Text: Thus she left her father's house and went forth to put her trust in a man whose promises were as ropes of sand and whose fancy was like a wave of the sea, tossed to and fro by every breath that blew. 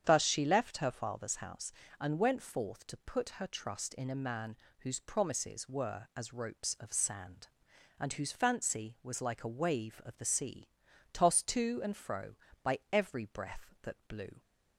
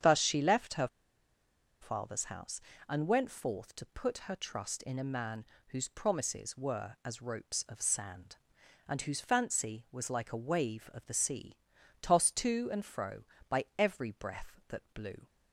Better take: first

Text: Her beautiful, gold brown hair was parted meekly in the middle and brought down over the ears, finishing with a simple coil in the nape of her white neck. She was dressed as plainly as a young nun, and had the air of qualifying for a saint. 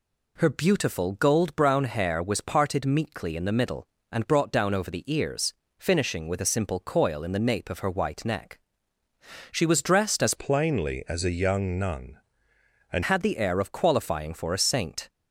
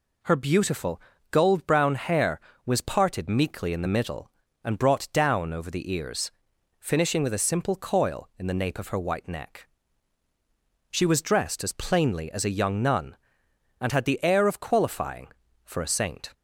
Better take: second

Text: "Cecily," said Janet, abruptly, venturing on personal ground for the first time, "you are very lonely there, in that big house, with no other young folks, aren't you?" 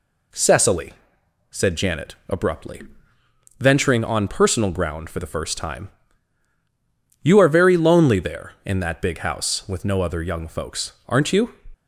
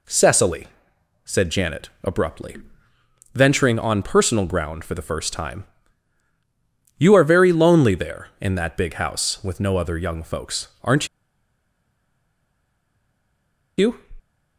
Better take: first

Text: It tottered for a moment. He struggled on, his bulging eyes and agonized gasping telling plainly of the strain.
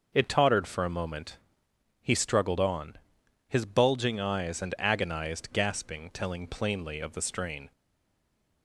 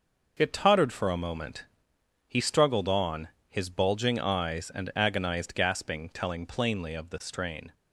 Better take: second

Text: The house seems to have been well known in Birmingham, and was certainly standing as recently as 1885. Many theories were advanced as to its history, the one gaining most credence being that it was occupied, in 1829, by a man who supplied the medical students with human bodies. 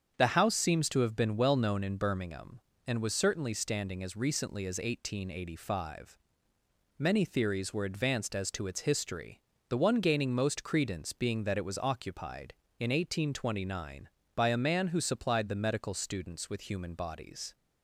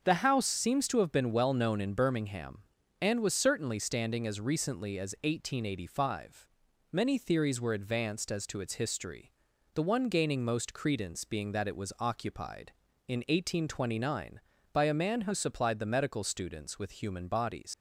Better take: first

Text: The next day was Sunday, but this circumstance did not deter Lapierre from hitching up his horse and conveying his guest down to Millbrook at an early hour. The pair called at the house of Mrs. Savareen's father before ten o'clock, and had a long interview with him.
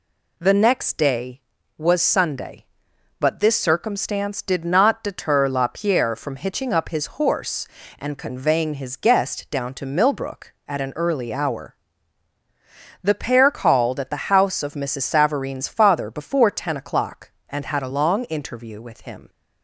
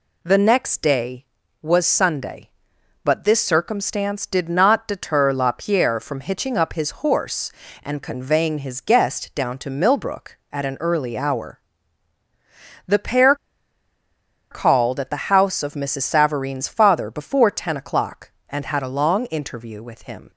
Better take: first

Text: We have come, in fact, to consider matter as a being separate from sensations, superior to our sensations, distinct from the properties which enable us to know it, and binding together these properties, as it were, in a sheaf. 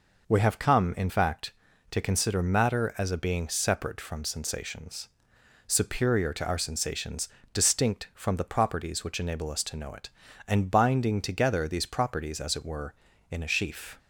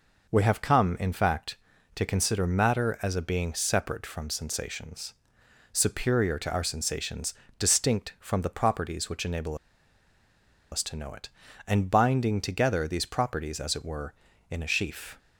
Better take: first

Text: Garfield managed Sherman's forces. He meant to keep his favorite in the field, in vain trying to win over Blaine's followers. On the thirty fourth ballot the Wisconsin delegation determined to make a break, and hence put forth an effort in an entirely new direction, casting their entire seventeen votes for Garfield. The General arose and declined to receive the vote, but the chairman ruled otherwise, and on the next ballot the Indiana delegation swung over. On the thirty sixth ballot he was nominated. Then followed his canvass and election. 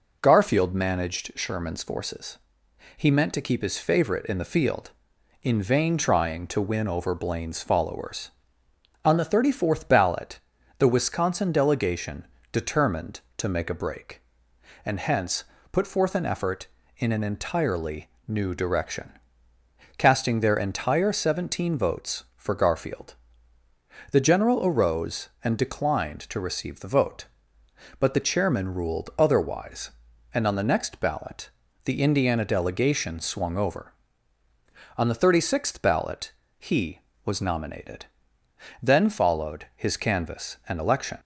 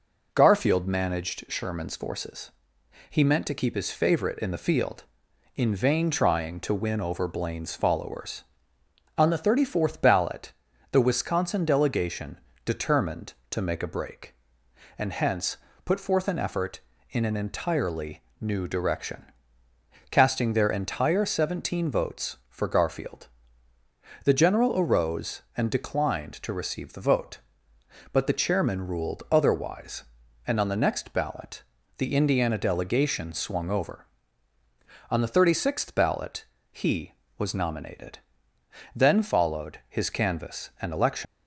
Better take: first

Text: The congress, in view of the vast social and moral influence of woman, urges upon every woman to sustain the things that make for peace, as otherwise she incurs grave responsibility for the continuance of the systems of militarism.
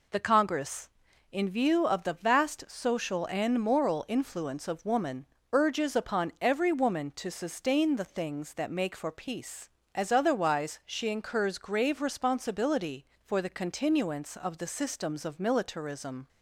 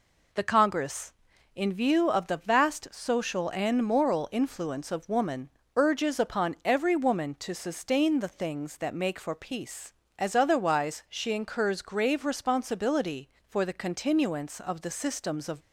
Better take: first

